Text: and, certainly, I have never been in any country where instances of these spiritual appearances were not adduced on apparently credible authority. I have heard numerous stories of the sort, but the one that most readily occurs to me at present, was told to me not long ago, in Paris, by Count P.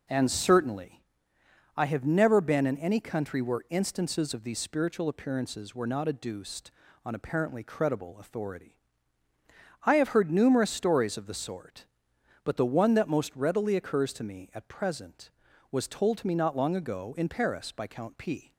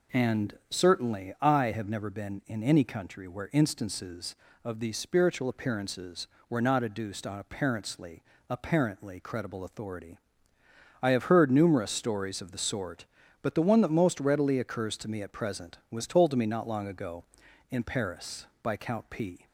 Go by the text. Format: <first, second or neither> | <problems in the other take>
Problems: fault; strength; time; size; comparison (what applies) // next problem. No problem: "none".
first | says "apparently" twice; at 8.4 s